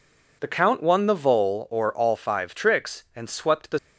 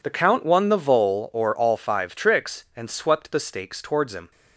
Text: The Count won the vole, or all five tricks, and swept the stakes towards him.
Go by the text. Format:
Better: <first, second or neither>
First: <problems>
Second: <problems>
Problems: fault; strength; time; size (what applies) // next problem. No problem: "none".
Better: second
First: stops before "stakes towards him"; at 3.7 s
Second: none